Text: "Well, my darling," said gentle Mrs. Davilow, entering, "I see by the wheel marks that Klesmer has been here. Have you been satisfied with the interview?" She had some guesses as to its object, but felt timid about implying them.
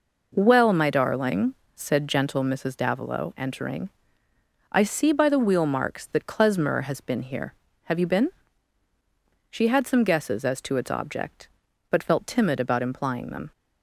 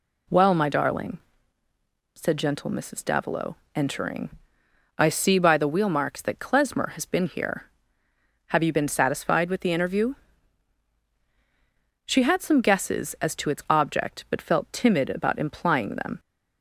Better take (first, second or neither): second